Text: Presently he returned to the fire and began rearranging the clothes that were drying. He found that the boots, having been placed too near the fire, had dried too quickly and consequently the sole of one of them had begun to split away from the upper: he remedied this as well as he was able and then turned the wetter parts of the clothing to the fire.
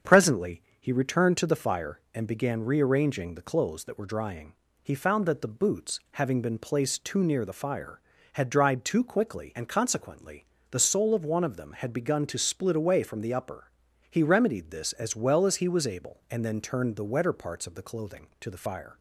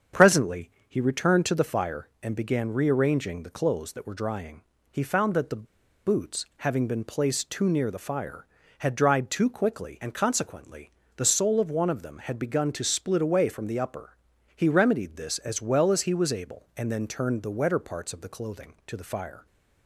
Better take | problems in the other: first | starts louder than the rest; strong; until 1.3 s; 7 dB; strong in the first // pauses between "Presently" and "he"; slight; at 0.7 s; 0.18 s long; slight in the first // pauses between "the" and "boots"; at 5.6 s; 0.39 s long // pauses between "consequently" and "the"; slight; at 10.8 s; 0.26 s long; slight in the first

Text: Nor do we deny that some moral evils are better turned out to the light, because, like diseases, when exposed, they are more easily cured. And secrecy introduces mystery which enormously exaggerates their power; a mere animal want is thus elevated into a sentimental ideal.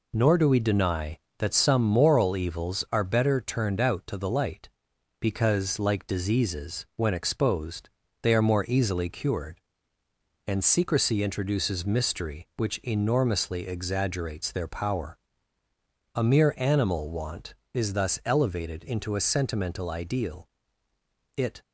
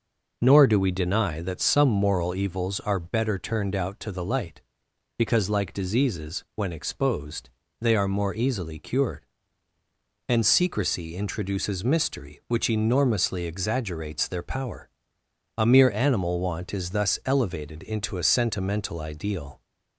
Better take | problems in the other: second | goes on to say "It"; slight; from 21.3 s on; 0.24 s long

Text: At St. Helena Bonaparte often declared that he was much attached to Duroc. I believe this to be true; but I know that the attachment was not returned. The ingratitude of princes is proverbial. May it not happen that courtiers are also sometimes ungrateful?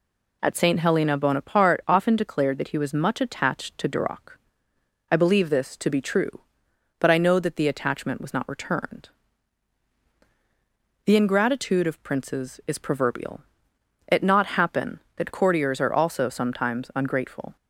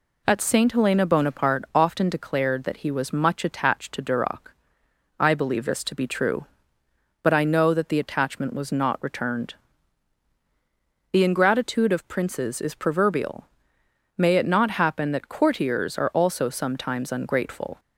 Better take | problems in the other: second | skips "May"; at 13.7 s

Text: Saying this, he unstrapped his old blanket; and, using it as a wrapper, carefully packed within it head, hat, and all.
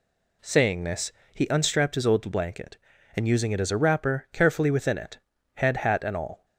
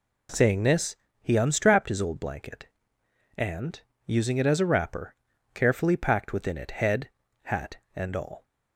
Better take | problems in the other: second | skips "packed"; at 4.7 s // pauses between "it" and "head"; slight; at 5.1 s; 0.36 s long

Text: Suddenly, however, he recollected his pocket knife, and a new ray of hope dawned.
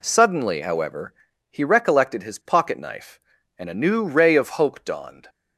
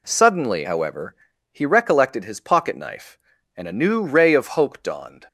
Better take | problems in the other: neither | none

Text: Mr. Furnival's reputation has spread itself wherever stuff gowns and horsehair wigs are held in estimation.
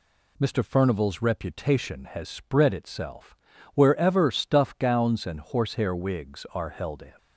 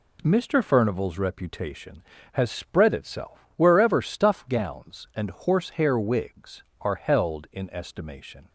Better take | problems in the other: second | pauses between "itself" and "wherever"; slight; at 3.3 s; 0.36 s long // stops before "estimation"; at 7.1 s

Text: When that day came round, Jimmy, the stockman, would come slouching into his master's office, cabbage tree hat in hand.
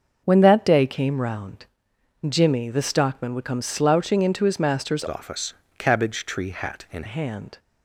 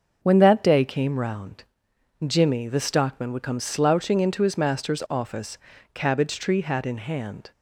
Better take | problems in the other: second | starts louder than the rest; until 1.2 s; 6 dB; also in the second // changes voice from "office" to "in"; from 5.0 to 7.0 s; 2.0 s long

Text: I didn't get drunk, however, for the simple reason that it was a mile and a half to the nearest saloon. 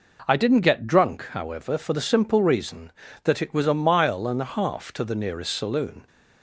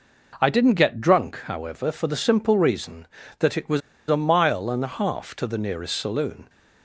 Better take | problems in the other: first | pauses between "was" and "a"; slight; at 3.8 s; 0.28 s long

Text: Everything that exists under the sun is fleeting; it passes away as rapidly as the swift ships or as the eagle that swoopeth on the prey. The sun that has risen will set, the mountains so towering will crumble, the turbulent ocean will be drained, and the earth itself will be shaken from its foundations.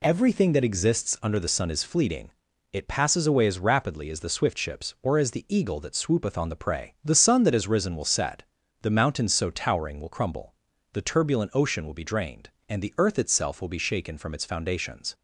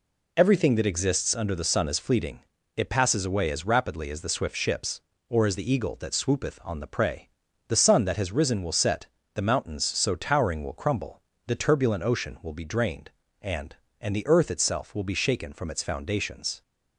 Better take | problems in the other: first | says "and" twice; at 13.9 s

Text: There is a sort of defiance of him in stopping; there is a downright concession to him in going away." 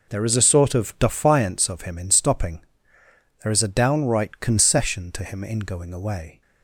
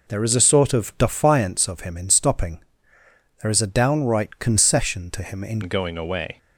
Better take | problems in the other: first | changes voice at "going"; from 5.6 s on; 0.7 s long

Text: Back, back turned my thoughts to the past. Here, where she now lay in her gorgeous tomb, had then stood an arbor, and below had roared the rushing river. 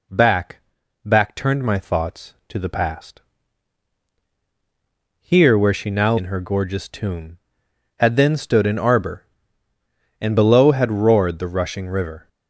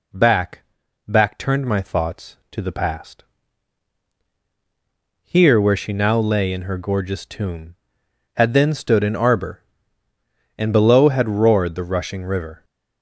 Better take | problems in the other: second | skips "lay"; at 6.1 s

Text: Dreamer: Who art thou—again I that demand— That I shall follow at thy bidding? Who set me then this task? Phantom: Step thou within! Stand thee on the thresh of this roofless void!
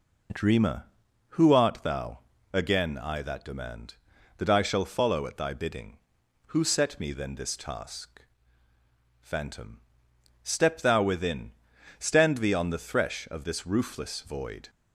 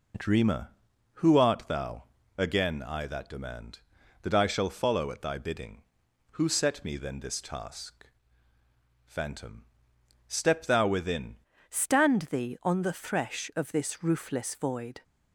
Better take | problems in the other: first | changes voice at "Stand"; from 11.6 s on; 3.4 s long

